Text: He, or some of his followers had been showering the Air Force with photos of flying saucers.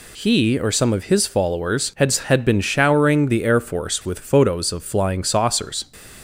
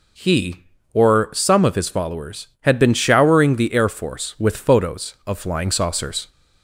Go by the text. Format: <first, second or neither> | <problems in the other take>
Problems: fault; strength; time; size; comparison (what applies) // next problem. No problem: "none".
second | says "had" twice; at 2.1 s